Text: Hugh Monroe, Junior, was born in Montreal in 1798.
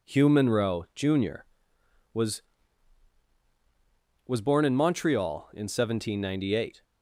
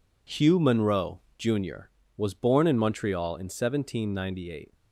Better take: second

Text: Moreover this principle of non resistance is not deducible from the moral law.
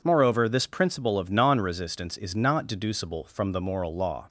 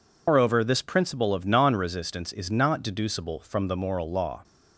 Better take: first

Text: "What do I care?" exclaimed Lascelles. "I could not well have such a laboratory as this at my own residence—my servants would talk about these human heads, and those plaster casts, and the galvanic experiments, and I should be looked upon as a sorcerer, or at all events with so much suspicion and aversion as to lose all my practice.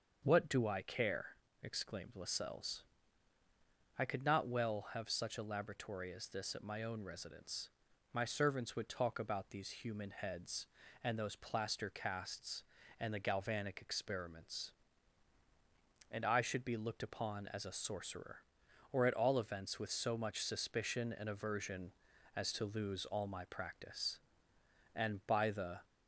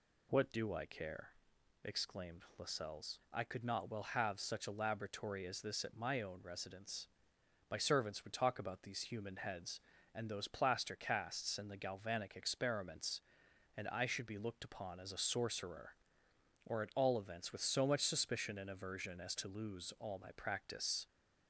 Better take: second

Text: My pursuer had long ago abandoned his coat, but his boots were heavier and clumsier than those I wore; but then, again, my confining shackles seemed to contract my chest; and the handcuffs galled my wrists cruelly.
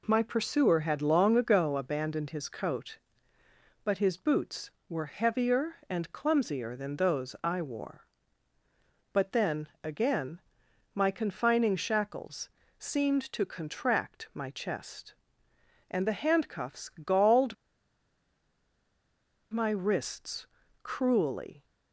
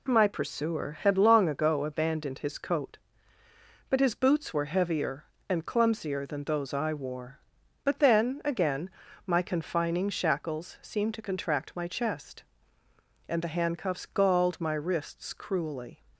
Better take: second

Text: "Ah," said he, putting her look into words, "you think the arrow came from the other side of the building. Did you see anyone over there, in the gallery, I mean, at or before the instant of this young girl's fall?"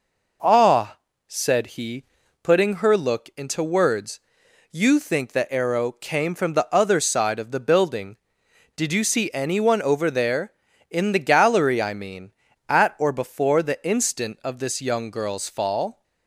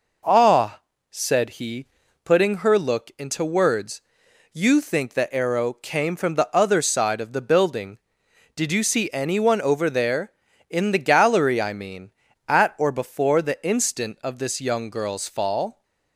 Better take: neither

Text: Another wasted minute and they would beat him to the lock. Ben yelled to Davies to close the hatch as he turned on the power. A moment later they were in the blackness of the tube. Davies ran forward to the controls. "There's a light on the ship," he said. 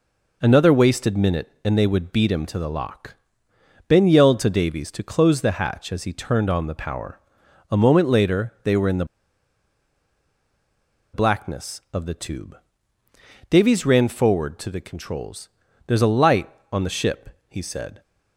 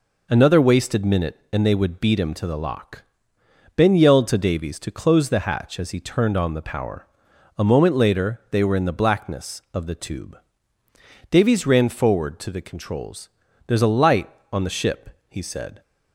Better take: second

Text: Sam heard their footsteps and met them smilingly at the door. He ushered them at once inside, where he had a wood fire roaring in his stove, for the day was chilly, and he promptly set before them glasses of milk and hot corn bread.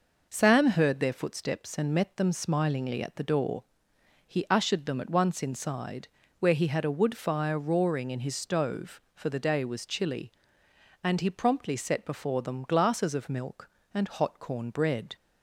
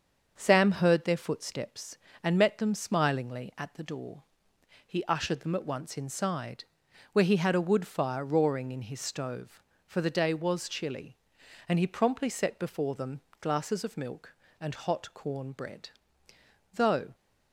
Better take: first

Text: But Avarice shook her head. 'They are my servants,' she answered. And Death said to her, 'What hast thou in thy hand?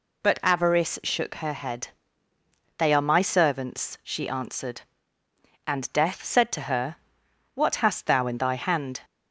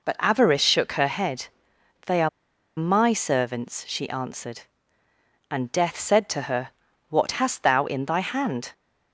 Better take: first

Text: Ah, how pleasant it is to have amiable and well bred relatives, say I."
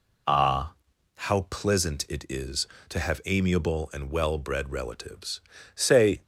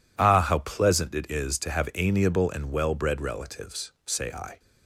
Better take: second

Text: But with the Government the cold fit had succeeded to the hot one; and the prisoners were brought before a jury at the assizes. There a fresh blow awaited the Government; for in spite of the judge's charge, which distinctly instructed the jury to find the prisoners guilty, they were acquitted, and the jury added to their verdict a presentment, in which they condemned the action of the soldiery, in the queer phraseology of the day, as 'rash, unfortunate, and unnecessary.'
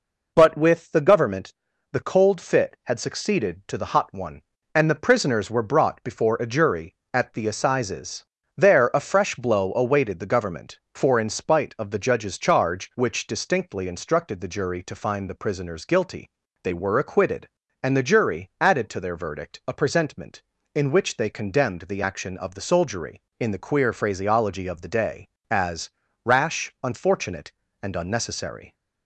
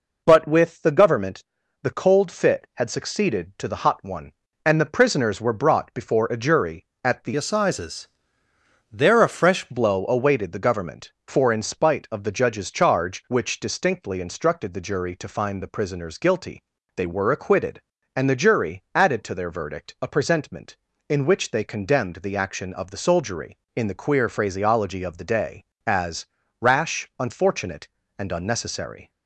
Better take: first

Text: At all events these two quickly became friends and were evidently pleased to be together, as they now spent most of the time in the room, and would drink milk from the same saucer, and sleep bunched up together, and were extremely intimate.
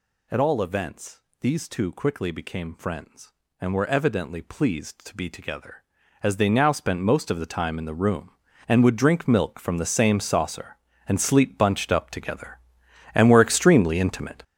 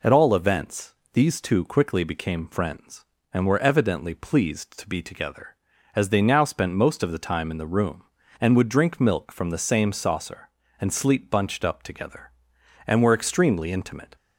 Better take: second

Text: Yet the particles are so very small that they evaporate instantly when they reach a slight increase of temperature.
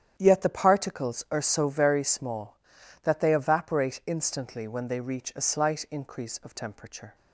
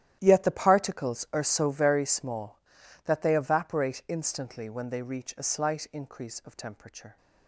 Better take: first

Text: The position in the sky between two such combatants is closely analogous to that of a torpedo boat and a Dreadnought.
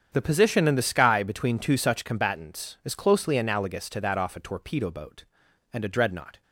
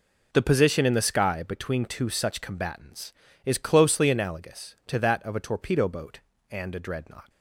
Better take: second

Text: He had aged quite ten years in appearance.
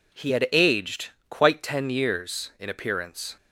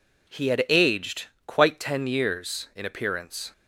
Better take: neither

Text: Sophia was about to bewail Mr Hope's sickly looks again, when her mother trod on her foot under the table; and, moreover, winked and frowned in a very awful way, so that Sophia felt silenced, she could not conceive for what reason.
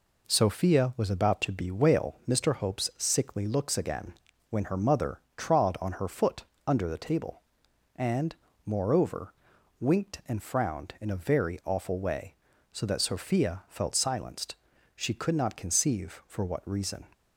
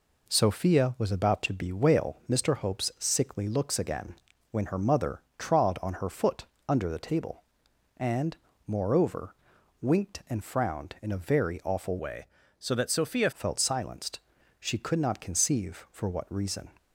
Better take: first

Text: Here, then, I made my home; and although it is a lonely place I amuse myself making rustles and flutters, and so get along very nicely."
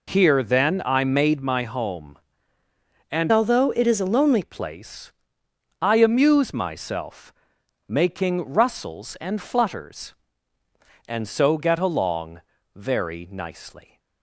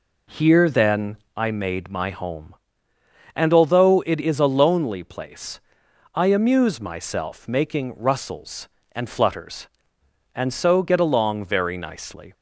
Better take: second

